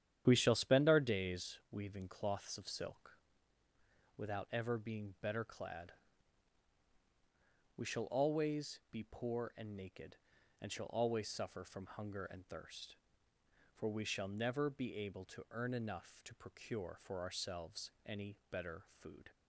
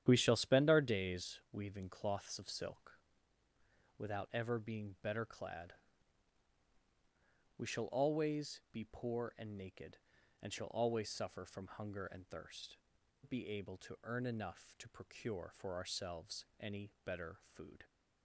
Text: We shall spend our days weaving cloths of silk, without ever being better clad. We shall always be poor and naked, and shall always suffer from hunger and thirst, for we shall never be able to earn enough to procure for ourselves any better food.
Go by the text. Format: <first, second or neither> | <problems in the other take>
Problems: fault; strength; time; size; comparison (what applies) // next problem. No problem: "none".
first | starts louder than the rest; strong; until 1.0 s; 10 dB; strong in the first // skips "for we shall never"; at 13.0 s // pauses between "ourselves" and "any"; slight; at 16.4 s; 0.16 s long; slight in the first